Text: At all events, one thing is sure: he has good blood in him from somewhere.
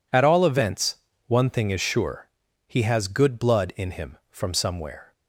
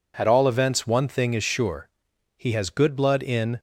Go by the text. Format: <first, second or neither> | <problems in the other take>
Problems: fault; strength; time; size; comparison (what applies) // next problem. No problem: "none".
first | stops before "him from somewhere"; at 3.5 s